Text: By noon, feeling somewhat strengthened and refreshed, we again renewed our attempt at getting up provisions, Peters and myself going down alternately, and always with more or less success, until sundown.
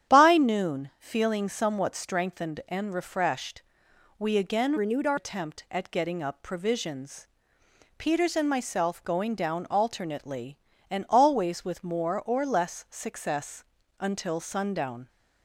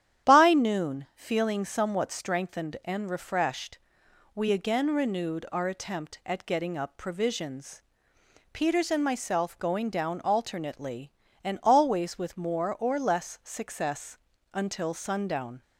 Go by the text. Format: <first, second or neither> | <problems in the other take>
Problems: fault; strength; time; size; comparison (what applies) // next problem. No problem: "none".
second | starts louder than the rest; strong; until 1.1 s; 9.5 dB; strong in the second // changes voice from "renewed" to "our"; from 4.7 to 5.1 s; 0.4 s long